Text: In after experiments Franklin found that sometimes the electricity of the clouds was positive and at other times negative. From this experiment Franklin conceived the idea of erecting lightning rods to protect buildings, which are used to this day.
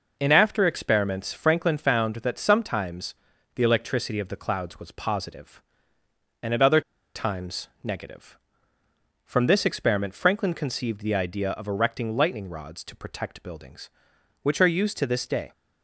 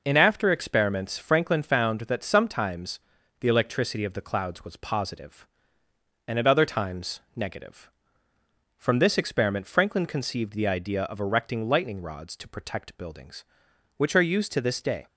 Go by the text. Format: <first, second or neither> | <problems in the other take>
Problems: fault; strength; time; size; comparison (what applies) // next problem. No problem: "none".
second | pauses between "sometimes" and "the"; at 3.1 s; 0.40 s long; also in the second // pauses between "other" and "times"; slight; at 6.8 s; 0.34 s long // pauses between "times" and "negative"; slight; at 7.6 s; 0.16 s long; slight in the second